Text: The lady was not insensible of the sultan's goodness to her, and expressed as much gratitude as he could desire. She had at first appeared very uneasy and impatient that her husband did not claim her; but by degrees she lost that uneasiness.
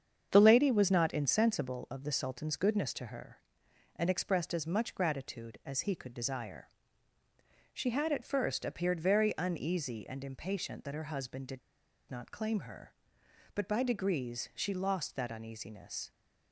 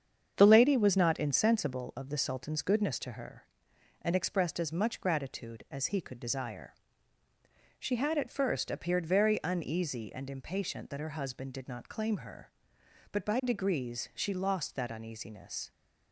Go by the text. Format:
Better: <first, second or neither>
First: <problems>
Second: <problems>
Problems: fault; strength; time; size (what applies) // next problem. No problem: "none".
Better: second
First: starts louder than the rest; strong; until 1.3 s; 7.5 dB // pauses between "did" and "not"; noticeable; at 11.5 s; 0.51 s long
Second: starts louder than the rest; strong; until 1.3 s; 7.5 dB